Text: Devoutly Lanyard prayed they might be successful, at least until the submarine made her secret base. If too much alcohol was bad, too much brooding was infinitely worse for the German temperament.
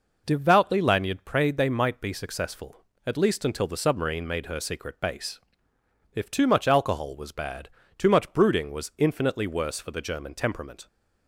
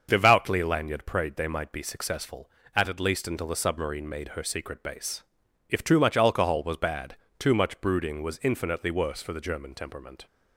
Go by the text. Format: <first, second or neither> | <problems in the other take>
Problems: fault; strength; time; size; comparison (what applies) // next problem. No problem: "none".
first | starts louder than the rest; until 1.1 s; 6.5 dB // says "at" twice; at 2.8 s